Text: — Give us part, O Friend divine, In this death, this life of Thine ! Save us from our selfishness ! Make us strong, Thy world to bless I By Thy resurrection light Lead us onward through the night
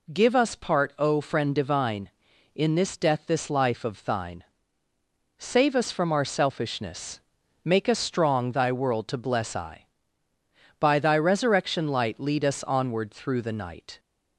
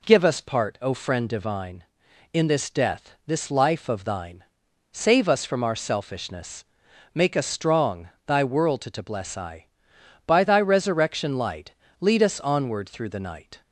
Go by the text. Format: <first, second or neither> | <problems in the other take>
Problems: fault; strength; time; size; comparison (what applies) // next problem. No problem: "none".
first | says "to" twice; at 8.9 s // pauses between "light" and "Lead"; slight; at 11.7 s; 0.26 s long